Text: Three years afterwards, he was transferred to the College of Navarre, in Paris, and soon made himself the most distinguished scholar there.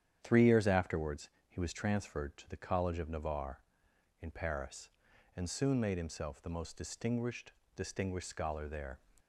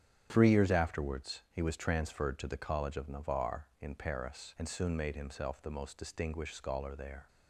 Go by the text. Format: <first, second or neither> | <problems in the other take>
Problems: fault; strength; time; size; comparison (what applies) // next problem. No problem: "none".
second | starts louder than the rest; strong; until 1.2 s; 9.5 dB; strong in the second // says "distinguished" twice; at 7.7 s